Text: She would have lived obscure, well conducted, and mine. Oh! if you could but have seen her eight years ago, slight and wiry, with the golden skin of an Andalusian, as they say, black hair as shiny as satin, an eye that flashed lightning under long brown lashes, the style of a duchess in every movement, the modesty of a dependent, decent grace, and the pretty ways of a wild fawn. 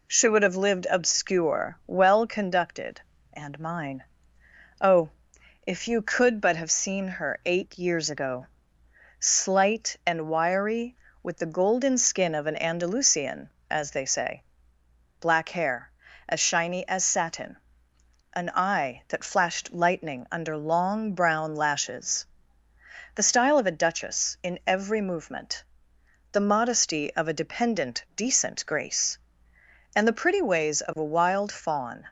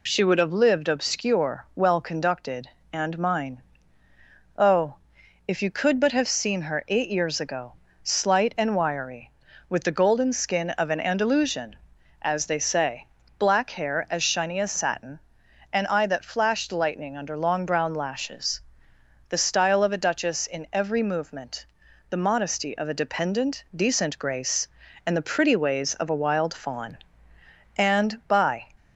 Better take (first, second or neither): first